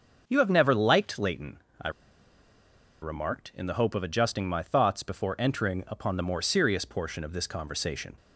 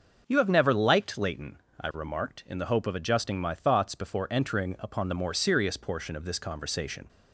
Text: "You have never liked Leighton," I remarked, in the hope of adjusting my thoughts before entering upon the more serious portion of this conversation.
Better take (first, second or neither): second